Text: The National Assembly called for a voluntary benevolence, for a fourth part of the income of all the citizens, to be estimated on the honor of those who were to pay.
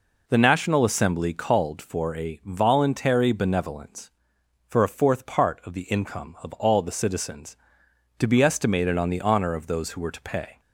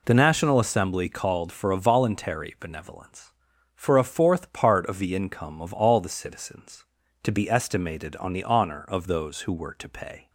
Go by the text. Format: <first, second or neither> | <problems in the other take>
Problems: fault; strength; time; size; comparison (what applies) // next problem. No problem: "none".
neither | none